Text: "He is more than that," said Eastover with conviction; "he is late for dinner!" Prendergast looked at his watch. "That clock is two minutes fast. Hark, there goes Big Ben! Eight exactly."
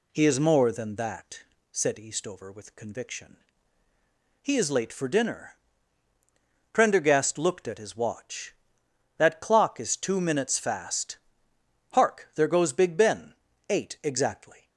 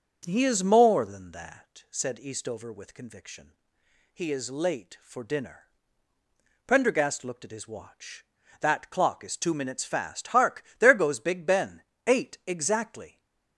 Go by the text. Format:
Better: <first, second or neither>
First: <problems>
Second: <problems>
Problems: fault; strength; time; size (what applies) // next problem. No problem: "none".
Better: first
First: none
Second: starts louder than the rest; until 1.7 s; 7 dB // stays silent after the last word; slight; from 13.0 s on; 0.5 s long